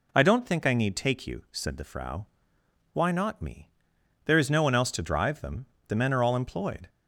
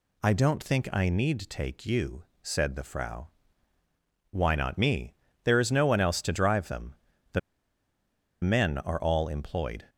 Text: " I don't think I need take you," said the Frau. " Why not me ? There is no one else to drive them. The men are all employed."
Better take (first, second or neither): first